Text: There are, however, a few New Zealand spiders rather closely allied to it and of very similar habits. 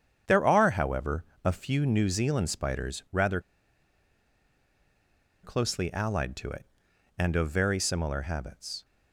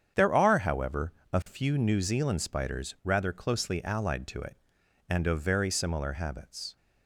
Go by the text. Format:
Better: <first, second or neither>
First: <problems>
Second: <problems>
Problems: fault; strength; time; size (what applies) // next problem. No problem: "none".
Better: second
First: starts louder than the rest; strong; until 1.4 s; 8 dB // pauses between "rather" and "closely"; strong; at 3.3 s; 2.0 s long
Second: starts louder than the rest; strong; until 1.3 s; 8 dB